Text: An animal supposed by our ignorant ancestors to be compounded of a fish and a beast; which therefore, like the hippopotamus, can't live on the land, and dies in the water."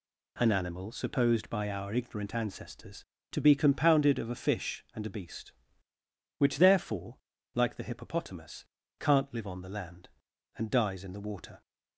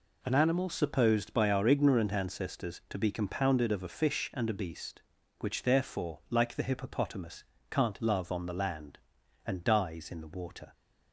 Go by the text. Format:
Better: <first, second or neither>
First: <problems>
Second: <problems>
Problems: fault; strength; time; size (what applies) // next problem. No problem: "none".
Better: first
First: none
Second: says "love" for "live"; at 8.0 s